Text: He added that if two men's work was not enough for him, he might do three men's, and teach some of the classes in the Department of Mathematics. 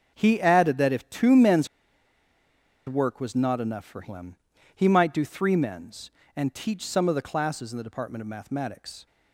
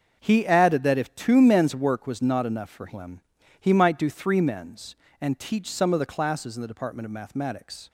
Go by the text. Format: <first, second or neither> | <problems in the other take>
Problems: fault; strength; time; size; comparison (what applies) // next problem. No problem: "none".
second | starts louder than the rest; until 1.1 s; 6.5 dB; also in the second // pauses between "men's" and "work"; at 1.6 s; 1.1 s long